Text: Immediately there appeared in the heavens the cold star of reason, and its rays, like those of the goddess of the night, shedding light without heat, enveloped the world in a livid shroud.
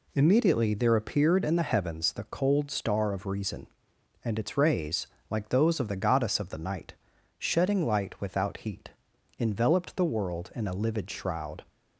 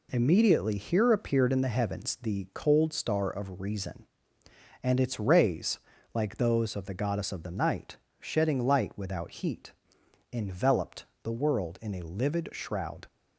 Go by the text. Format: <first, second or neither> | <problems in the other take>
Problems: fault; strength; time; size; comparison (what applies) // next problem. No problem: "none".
first | says "here" for "there"; at 0.7 s // pauses between "enveloped" and "the"; slight; at 11.0 s; 0.18 s long